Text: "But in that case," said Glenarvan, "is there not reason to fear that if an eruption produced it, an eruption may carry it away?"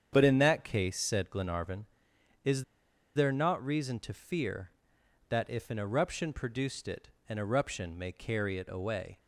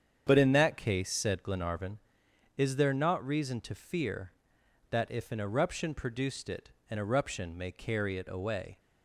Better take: second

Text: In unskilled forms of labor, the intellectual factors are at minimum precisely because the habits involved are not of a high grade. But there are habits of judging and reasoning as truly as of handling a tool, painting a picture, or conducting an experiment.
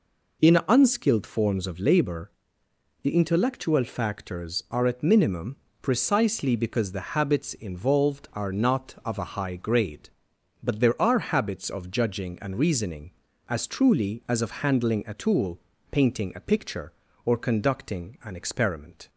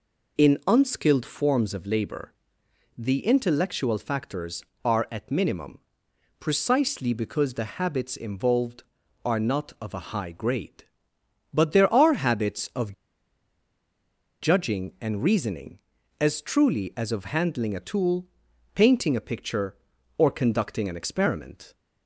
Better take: first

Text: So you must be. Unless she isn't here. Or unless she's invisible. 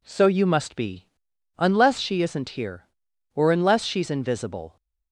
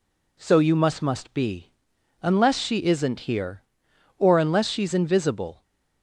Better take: first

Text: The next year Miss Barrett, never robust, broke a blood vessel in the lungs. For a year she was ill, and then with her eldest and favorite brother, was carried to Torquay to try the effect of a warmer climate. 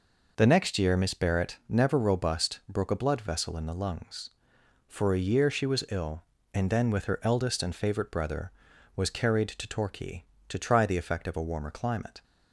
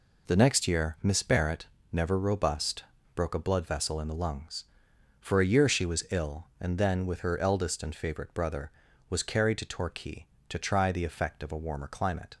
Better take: neither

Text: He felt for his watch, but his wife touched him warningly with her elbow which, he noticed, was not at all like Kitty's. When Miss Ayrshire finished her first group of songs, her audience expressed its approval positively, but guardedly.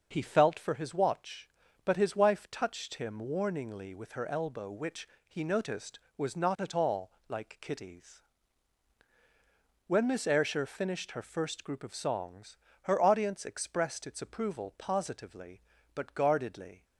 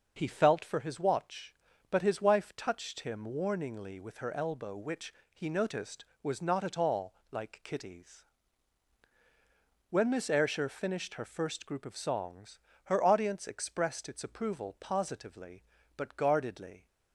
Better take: neither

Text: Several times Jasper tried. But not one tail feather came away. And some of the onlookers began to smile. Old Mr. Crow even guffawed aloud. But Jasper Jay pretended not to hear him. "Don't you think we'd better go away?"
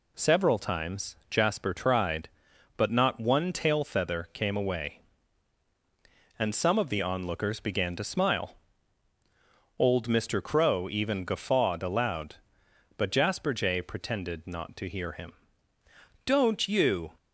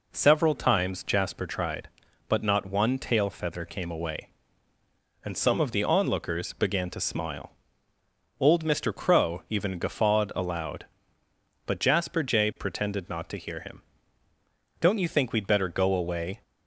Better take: second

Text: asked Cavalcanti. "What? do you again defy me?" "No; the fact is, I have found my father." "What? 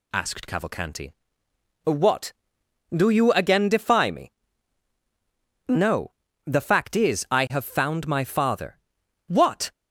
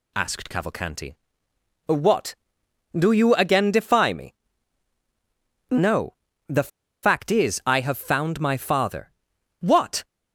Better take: first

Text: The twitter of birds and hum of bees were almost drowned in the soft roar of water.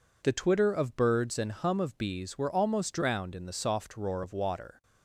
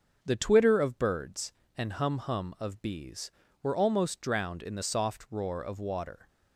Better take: first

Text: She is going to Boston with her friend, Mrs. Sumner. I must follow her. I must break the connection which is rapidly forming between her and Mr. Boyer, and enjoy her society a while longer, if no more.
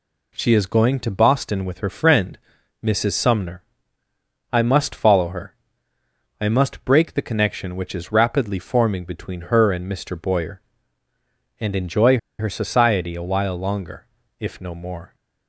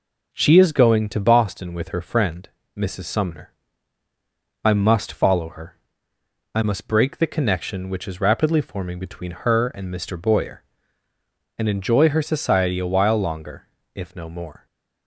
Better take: second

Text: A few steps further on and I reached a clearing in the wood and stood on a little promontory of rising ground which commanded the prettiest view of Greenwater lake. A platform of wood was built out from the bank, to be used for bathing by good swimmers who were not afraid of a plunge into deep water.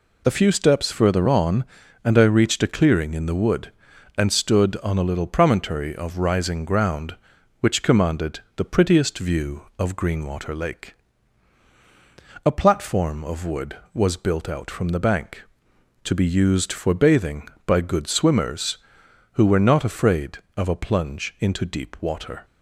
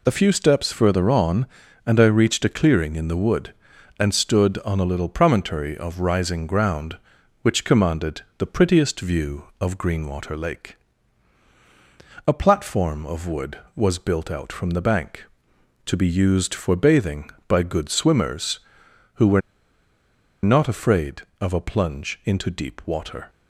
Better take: first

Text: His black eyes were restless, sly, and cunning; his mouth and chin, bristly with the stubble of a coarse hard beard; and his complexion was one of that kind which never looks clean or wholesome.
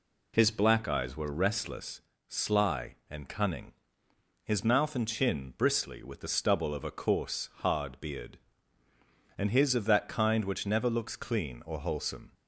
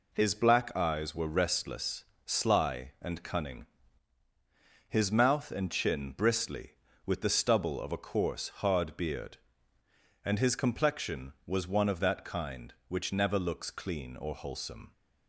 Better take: second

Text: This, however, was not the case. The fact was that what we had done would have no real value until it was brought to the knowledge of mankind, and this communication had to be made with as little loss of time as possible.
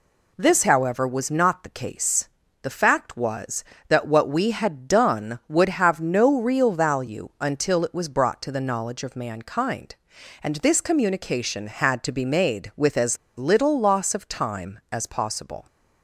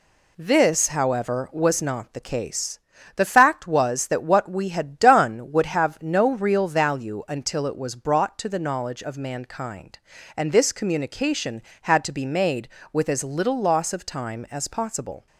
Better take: second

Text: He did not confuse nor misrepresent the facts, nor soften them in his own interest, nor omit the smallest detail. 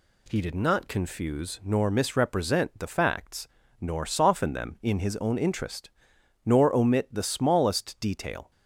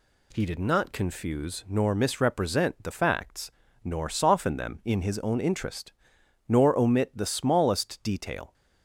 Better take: neither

